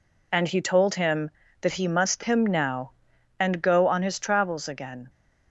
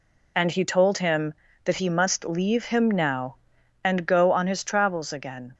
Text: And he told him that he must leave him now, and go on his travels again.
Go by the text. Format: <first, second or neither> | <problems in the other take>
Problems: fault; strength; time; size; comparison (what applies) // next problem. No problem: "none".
second | skips "leave"; at 2.2 s